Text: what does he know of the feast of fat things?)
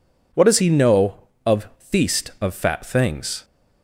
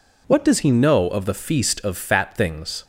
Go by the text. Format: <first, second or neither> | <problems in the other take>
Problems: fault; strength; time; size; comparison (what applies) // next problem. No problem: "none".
second | skips "the"; at 1.7 s